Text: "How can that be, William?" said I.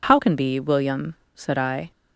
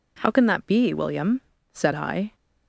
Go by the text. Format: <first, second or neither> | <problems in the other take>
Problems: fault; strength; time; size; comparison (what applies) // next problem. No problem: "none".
second | skips "that"; at 0.3 s